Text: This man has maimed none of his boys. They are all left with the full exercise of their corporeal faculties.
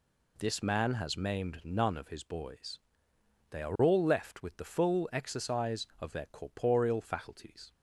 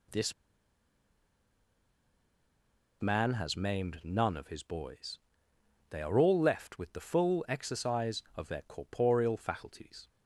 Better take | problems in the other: first | pauses between "This" and "man"; strong; at 0.3 s; 2.6 s long

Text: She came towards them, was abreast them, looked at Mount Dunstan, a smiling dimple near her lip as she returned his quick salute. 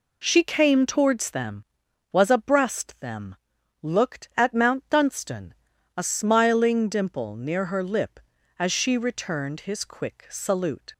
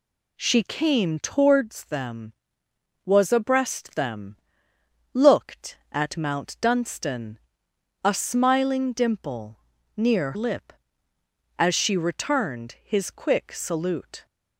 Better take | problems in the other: first | pauses between "dimple" and "near"; at 9.5 s; 0.38 s long // skips "her"; at 10.3 s

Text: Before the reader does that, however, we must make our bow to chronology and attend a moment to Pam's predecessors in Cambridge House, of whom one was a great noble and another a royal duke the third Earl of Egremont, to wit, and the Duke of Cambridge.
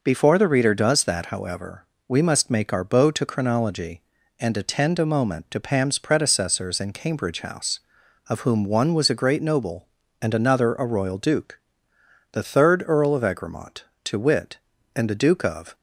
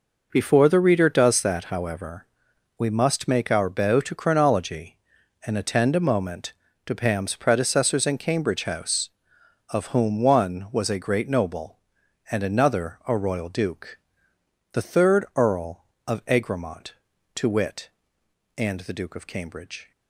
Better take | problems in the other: second | pauses between "duke" and "the"; noticeable; at 11.5 s; 0.74 s long; noticeable in the second // stops before "Cambridge"; at 15.7 s

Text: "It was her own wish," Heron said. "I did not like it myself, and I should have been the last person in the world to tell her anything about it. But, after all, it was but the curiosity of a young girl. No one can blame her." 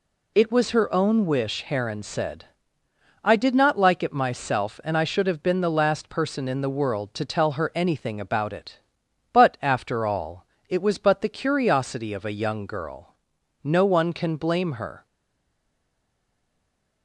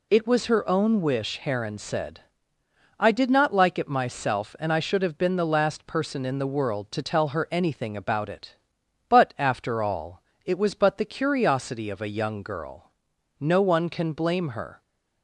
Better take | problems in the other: second | stays silent after the last word; noticeable; from 15.0 s on; 2.0 s long

